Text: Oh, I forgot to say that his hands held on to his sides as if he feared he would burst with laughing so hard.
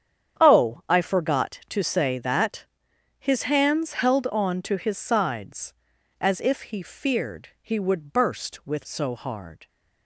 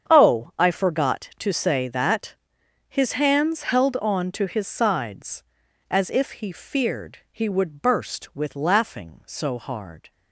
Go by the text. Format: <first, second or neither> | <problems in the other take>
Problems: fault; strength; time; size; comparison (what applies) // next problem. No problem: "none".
second | starts louder than the rest; strong; until 1.4 s; 8.5 dB; strong in the second // pauses between "that" and "his"; noticeable; at 2.6 s; 0.52 s long; noticeable in the second // skips "laughing"; at 8.8 s